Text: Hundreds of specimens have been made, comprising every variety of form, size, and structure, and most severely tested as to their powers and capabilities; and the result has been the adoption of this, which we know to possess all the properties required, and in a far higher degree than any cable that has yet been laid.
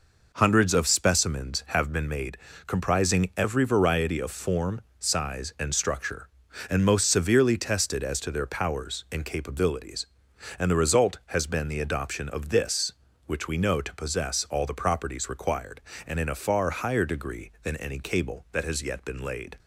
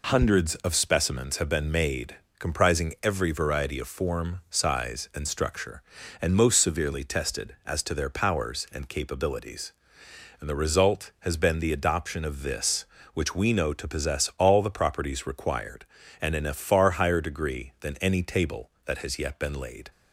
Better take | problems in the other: first | says "table" for "cable"; at 18.2 s

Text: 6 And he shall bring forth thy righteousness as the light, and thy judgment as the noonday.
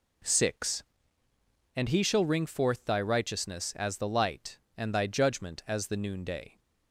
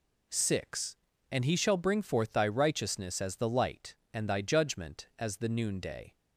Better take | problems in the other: second | says "ring" for "bring"; at 2.2 s

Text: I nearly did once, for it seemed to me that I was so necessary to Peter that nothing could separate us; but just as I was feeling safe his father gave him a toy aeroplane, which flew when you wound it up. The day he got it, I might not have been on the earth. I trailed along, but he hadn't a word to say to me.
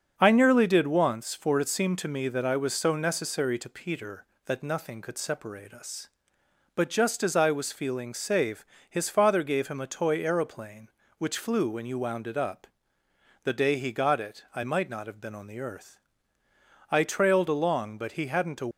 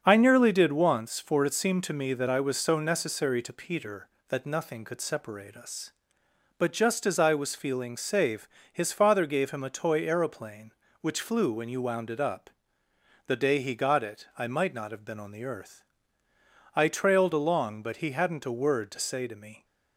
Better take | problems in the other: second | starts louder than the rest; until 1.1 s; 7 dB; also in the second // pauses between "safe" and "his"; slight; at 8.6 s; 0.24 s long; slight in the second // stops before "word to say to me"; at 18.7 s

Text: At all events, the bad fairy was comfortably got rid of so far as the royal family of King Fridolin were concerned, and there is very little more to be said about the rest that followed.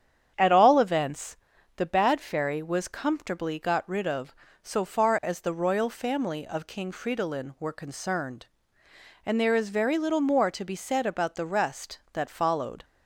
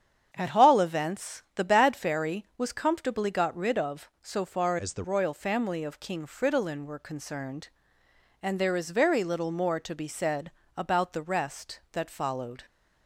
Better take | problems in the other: first | starts louder than the rest; strong; until 1.3 s; 8 dB; strong in the first // changes voice from "as" to "the"; from 4.7 to 5.0 s; 0.3 s long // pauses between "said" and "about"; slight; at 10.5 s; 0.26 s long

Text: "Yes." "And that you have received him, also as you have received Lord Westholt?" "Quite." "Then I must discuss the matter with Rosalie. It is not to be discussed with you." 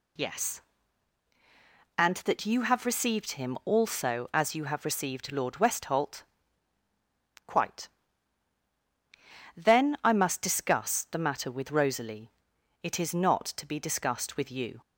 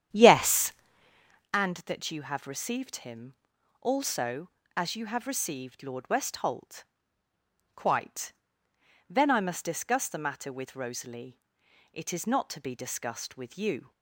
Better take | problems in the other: first | starts louder than the rest; strong; until 1.5 s; 9.5 dB

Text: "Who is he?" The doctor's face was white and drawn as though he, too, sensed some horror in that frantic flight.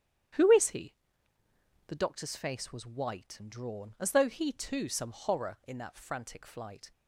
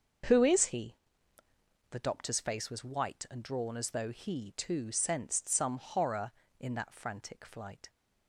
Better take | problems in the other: second | starts louder than the rest; strong; until 2.2 s; 9.5 dB; also in the second // skips "sensed"; at 4.8 s

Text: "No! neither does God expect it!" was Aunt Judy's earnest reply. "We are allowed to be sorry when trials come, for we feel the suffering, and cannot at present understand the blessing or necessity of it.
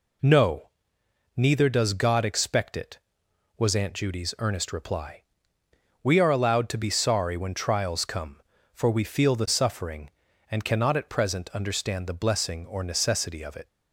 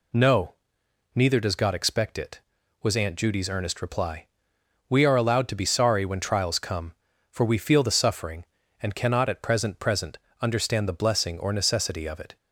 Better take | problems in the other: first | says "present" twice; at 9.8 s

